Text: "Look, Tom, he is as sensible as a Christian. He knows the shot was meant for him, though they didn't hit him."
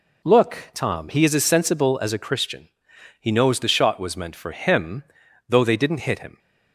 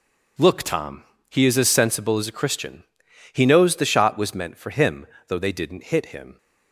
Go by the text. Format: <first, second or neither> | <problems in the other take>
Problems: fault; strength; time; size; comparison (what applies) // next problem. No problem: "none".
neither | none